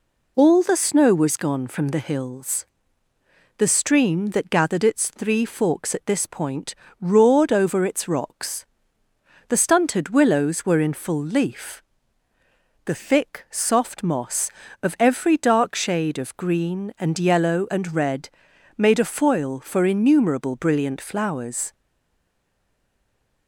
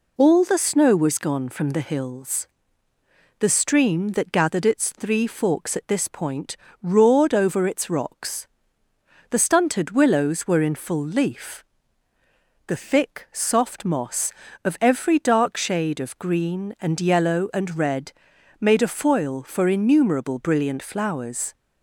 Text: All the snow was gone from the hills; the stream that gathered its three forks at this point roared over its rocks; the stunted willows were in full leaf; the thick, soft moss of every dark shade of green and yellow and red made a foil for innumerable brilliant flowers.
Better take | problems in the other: second | pauses between "point" and "roared"; slight; at 6.7 s; 0.24 s long; slight in the second // pauses between "red" and "made"; noticeable; at 18.2 s; 0.48 s long; noticeable in the second // stays silent after the last word; noticeable; from 21.7 s on; 1.7 s long

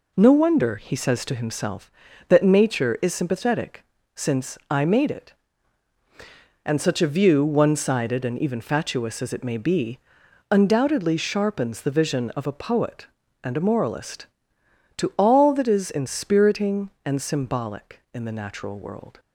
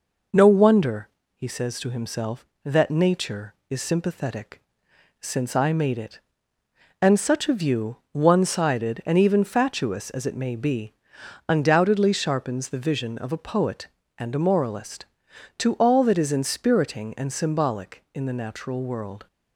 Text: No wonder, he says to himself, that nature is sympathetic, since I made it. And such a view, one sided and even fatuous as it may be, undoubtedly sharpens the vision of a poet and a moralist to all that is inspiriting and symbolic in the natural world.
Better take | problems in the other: neither | none

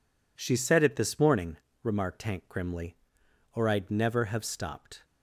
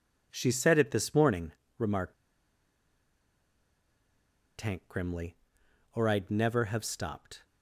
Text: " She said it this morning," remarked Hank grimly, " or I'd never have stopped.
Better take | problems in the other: first | pauses between "remarked" and "Hank"; strong; at 2.1 s; 2.4 s long

